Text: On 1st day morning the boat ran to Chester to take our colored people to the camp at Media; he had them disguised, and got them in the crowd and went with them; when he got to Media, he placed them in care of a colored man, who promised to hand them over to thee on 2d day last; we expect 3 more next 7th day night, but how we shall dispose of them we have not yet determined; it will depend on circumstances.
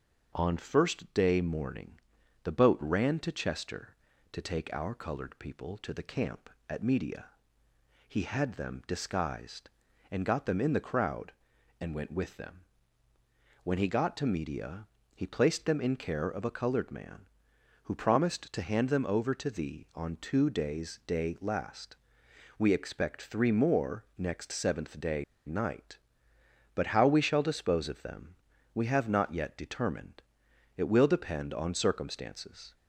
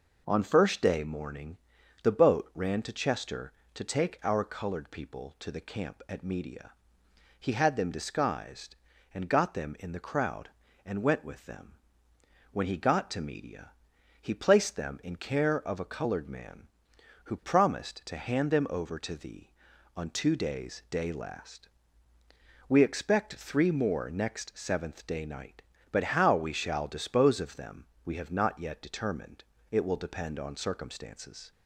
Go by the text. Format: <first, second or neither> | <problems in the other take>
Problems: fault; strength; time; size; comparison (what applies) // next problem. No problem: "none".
second | starts louder than the rest; until 1.3 s; 6.5 dB // pauses between "morning" and "the"; at 1.9 s; 0.42 s long; also in the second // pauses between "day" and "night"; slight; at 25.2 s; 0.22 s long // pauses between "them" and "we"; at 28.3 s; 0.38 s long; slight in the second